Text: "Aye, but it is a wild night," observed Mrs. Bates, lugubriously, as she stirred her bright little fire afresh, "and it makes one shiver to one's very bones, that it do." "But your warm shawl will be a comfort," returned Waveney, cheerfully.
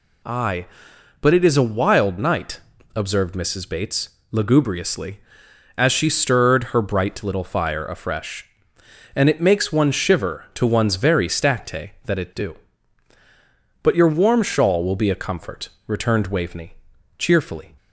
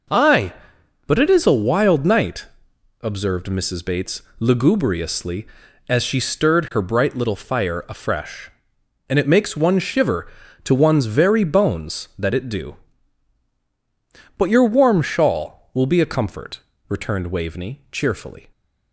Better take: second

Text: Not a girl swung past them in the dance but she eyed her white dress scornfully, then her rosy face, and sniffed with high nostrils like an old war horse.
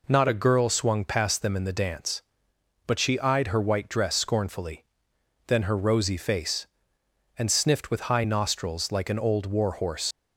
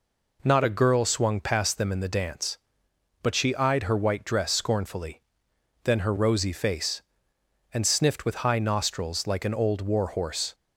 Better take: second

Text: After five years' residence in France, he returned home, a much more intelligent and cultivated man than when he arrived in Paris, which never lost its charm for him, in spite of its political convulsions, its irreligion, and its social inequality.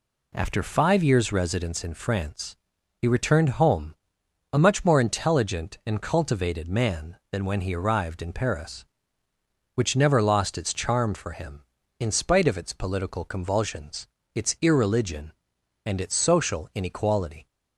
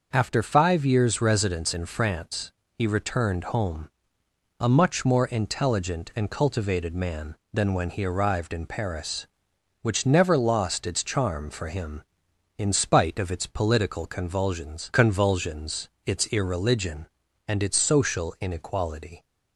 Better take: first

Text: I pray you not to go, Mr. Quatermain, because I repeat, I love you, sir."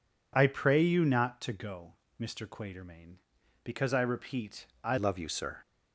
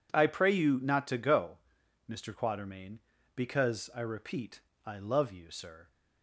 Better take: second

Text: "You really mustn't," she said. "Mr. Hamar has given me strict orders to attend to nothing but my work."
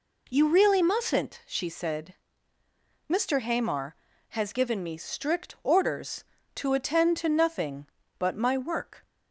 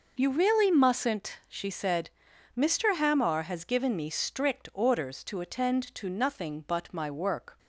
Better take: neither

